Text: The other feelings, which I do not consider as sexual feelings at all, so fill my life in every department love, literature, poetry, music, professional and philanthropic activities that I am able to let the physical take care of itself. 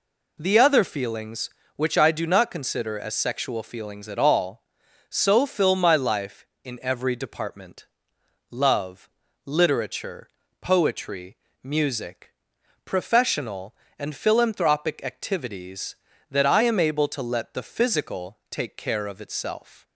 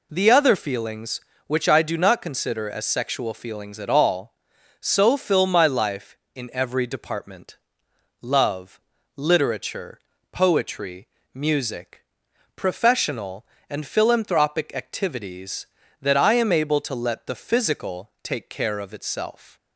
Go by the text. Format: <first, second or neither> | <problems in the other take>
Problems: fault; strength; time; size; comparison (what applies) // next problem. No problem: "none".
neither | pauses between "department" and "love"; noticeable; the same in both